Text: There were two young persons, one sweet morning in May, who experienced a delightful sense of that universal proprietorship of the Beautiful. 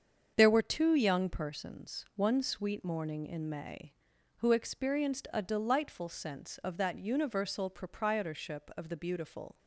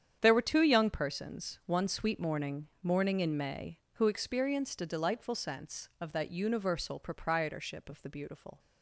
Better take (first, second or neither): first